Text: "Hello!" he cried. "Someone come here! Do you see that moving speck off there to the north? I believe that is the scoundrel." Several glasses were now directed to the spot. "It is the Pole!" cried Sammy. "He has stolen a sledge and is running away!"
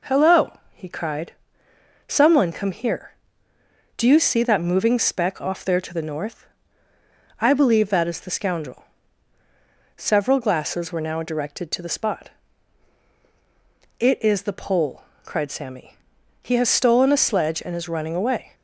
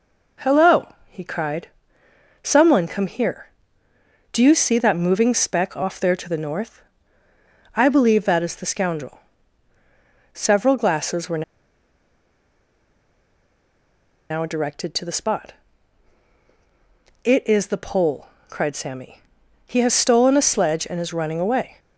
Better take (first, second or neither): first